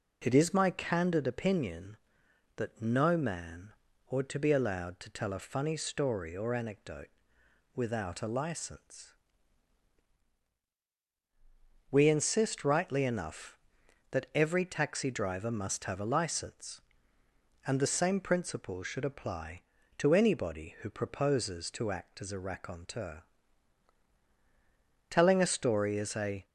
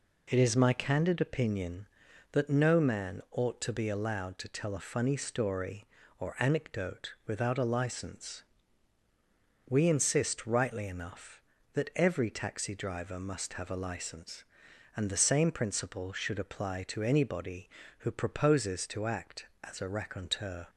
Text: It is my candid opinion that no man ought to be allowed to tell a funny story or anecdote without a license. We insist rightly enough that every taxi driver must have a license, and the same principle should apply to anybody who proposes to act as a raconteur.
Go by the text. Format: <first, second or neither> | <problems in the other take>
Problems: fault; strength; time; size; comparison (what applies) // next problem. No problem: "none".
second | pauses between "man" and "ought"; at 3.7 s; 0.38 s long // pauses between "anecdote" and "without"; noticeable; at 7.0 s; 0.66 s long // goes on to say "Telling a story is a"; from 25.1 s on; 1.3 s long